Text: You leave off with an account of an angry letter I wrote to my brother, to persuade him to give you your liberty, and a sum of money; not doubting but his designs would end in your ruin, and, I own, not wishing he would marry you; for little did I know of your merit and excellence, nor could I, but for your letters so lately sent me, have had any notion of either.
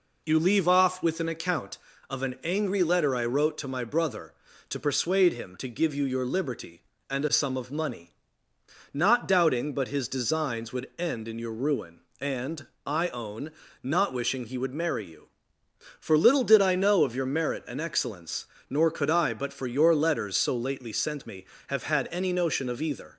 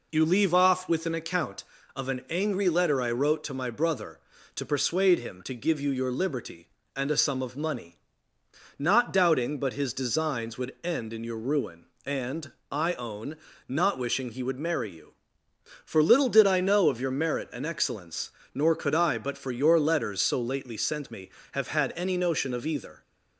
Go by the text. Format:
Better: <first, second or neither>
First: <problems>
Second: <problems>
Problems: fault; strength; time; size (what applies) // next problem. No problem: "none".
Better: neither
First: none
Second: none